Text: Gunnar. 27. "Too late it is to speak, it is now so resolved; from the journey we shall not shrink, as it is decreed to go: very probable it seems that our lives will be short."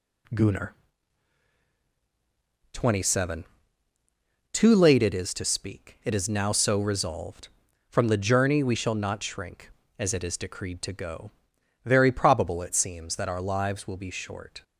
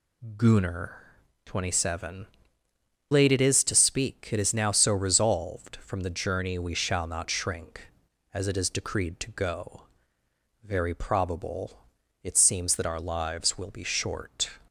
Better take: first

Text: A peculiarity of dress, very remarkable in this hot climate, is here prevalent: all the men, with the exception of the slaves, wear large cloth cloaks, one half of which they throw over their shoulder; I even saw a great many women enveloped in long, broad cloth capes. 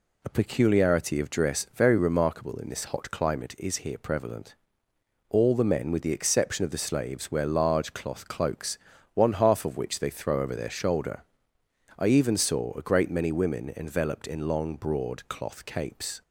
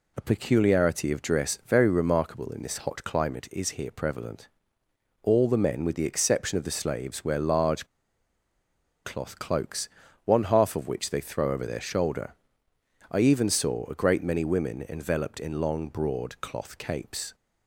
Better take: first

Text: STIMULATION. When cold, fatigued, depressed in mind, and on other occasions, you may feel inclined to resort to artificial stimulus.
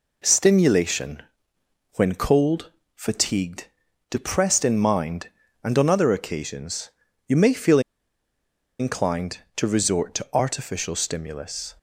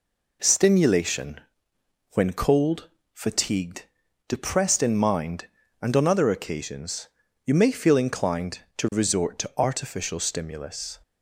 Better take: second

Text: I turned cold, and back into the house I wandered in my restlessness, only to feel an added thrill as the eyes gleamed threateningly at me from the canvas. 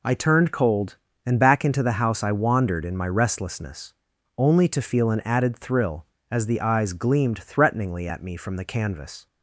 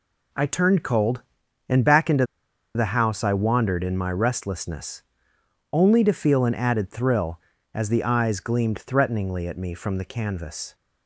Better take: first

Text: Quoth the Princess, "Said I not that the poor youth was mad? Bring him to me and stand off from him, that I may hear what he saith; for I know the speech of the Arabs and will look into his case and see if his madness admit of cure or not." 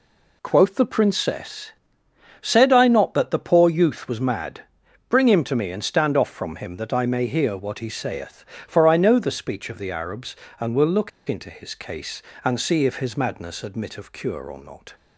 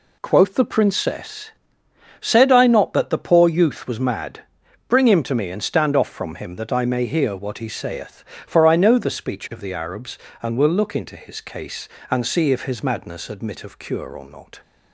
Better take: second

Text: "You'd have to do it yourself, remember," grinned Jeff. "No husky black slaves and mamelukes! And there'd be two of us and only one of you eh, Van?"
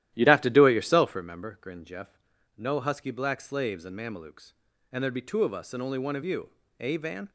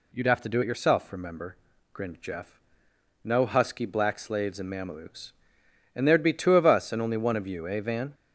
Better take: second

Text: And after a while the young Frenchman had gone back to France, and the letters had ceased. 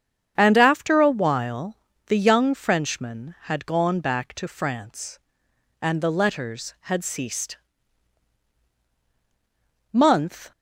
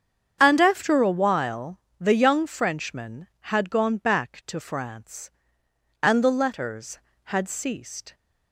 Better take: second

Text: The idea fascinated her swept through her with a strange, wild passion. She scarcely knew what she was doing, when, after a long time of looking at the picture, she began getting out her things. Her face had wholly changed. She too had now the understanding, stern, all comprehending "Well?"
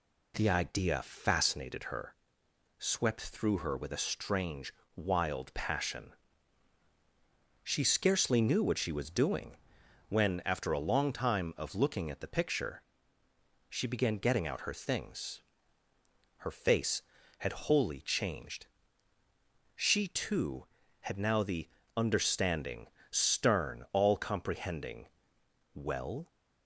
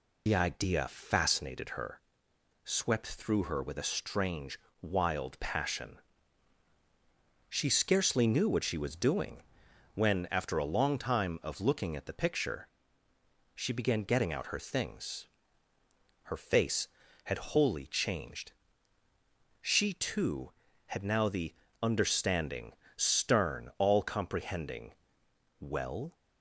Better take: first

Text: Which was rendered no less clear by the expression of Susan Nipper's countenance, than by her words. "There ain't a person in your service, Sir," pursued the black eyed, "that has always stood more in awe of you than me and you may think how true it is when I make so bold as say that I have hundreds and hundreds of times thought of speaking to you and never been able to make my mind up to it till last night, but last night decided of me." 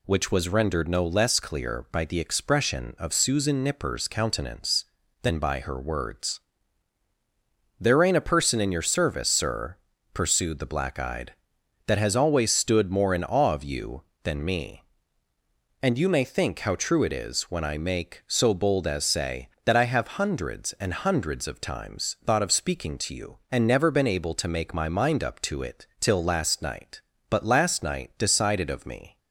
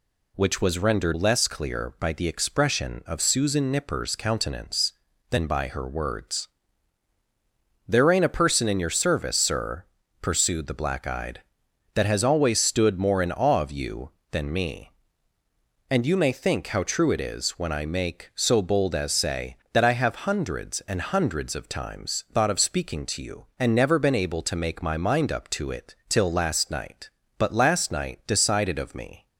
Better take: first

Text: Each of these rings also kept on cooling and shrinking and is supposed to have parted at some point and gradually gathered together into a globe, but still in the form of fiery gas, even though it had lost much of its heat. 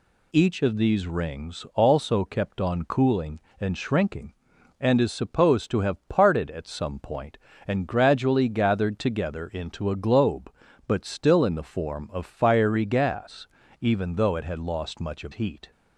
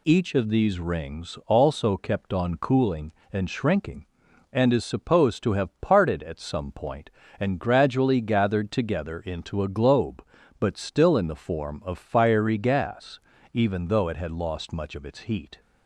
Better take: second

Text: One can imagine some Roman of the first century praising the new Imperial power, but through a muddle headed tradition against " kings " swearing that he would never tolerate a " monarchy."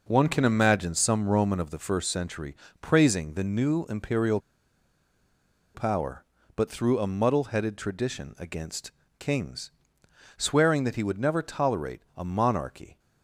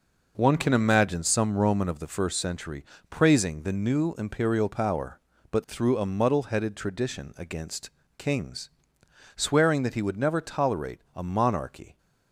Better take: second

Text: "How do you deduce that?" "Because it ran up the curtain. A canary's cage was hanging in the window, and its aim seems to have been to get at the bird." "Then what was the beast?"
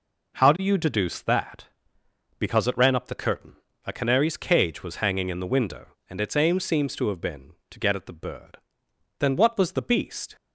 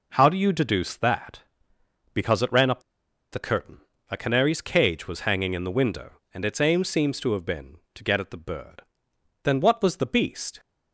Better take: first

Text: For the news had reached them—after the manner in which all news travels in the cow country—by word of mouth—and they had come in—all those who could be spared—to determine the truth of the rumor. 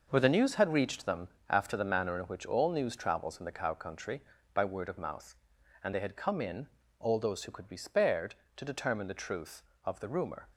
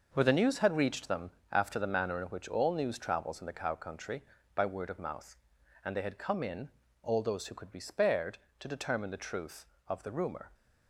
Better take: neither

